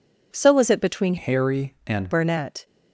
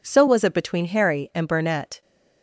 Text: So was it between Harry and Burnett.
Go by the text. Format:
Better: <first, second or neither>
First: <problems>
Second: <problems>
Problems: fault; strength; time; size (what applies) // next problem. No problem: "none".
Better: second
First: changes voice from "Harry" to "and"; from 1.1 to 2.1 s; 1.0 s long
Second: none